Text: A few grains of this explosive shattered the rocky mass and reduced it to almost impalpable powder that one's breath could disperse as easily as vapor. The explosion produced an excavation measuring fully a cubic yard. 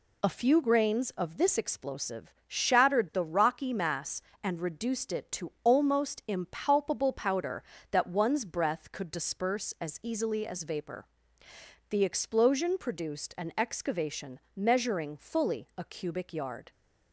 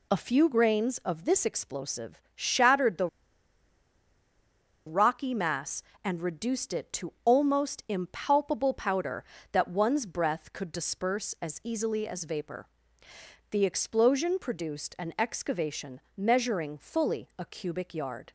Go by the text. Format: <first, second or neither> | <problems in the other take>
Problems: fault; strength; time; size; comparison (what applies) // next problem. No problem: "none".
first | pauses between "the" and "rocky"; strong; at 3.0 s; 1.7 s long // pauses between "excavation" and "measuring"; slight; at 15.9 s; 0.16 s long; slight in the first